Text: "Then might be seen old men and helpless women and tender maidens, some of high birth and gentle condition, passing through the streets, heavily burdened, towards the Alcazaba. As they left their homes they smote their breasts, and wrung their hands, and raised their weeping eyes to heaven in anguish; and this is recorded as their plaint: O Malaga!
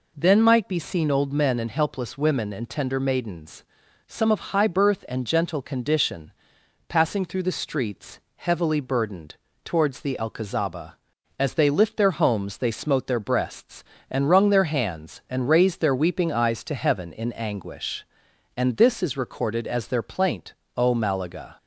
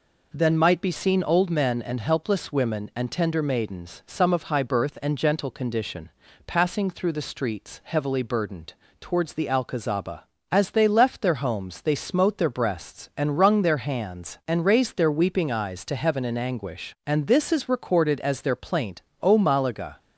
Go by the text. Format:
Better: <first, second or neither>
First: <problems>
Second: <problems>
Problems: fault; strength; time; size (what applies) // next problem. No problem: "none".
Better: second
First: says "lift" for "left"; at 11.6 s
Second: none